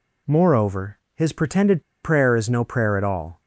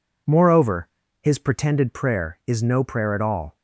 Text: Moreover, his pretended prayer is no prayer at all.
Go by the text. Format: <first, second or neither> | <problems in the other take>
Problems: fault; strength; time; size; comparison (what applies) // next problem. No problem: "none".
second | pauses between "pretended" and "prayer"; slight; at 1.8 s; 0.20 s long